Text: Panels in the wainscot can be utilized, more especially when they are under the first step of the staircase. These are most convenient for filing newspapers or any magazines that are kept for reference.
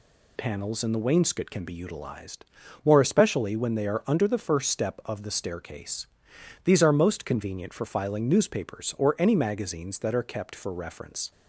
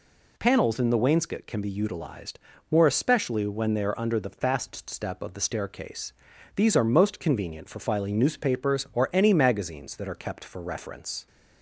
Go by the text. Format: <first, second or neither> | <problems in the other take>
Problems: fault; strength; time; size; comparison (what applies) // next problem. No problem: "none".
first | says "fast" for "first"; at 4.3 s